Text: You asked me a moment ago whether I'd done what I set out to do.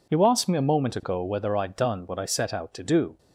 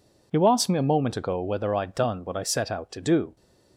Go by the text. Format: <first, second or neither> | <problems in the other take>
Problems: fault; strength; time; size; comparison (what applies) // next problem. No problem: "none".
neither | none